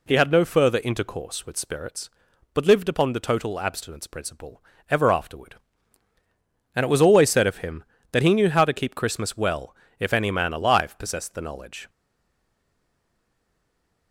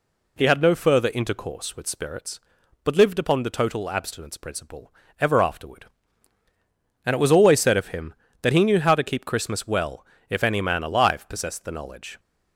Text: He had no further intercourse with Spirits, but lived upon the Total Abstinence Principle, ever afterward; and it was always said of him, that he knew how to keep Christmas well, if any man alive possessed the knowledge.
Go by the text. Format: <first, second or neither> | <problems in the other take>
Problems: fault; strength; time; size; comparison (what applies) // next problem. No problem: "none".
second | stays silent after the last word; from 11.8 s on; 2.3 s long